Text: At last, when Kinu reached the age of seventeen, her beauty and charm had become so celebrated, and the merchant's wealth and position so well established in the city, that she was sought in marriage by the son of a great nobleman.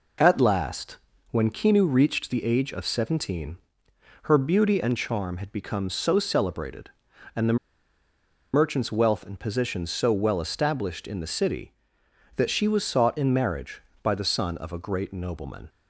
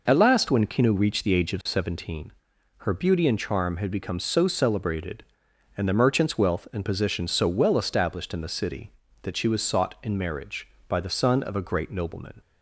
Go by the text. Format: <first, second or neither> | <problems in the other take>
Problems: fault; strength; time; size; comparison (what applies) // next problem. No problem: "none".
second | pauses between "the" and "merchant's"; noticeable; at 7.5 s; 0.96 s long